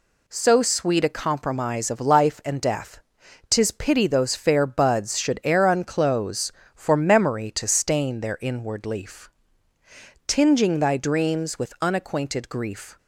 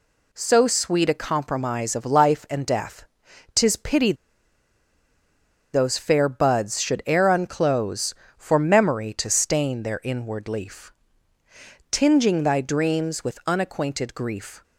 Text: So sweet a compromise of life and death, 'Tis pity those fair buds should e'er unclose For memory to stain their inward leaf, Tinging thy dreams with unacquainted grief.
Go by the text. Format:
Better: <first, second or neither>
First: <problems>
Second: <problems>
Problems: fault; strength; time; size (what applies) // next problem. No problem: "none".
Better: first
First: none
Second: pauses between "pity" and "those"; strong; at 4.1 s; 1.6 s long